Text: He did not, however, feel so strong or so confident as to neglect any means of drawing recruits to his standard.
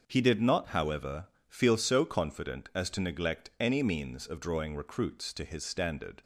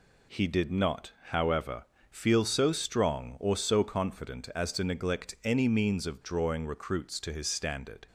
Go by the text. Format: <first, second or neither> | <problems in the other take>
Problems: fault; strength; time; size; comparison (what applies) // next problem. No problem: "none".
second | starts louder than the rest; until 1.0 s; 6.5 dB // skips "so strong or"; at 1.7 s